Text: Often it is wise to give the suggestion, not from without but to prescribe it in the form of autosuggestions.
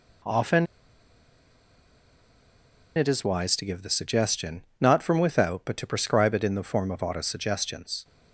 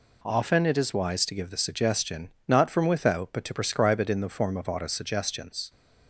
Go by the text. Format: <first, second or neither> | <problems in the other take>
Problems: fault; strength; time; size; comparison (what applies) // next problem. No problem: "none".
second | pauses between "Often" and "it"; strong; at 0.6 s; 2.3 s long